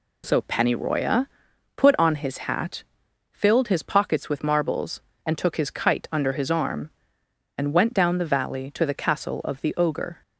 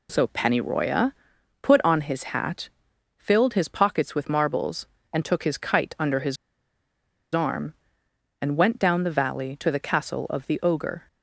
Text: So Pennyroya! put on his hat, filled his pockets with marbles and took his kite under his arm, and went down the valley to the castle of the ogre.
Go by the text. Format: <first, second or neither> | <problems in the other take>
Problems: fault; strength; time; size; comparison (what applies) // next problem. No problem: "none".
first | pauses between "his" and "arm"; noticeable; at 6.3 s; 0.96 s long